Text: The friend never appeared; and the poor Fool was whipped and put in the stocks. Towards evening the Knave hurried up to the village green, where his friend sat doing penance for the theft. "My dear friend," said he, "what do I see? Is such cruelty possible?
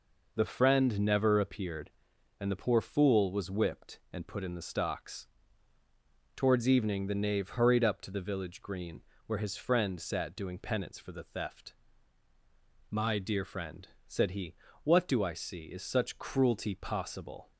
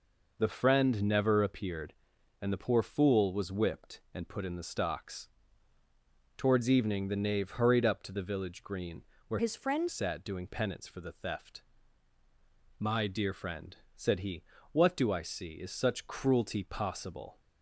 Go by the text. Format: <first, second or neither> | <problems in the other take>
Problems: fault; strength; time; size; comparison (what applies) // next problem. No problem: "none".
first | changes voice from "his" to "friend"; from 9.3 to 9.8 s; 0.5 s long